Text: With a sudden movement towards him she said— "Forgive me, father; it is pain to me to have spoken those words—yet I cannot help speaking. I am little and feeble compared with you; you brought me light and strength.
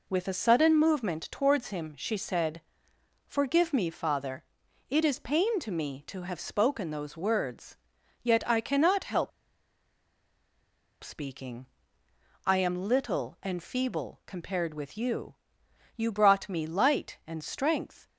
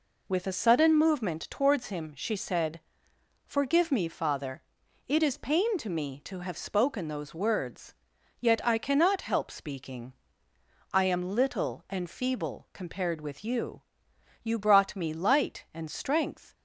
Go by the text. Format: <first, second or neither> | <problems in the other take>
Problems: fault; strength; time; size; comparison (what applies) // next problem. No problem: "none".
second | pauses between "help" and "speaking"; strong; at 9.3 s; 1.7 s long